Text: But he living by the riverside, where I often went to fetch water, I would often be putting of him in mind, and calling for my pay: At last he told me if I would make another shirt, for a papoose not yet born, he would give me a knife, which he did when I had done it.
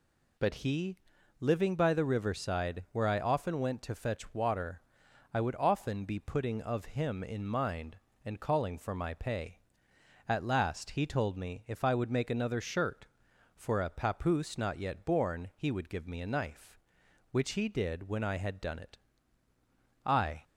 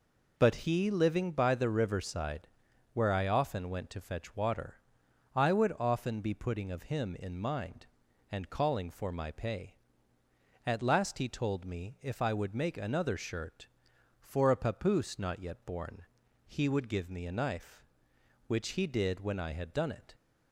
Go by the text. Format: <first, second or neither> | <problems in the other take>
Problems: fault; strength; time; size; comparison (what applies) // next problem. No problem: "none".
second | pauses between "he" and "living"; at 0.9 s; 0.42 s long // goes on to say "I"; slight; from 20.0 s on; 0.38 s long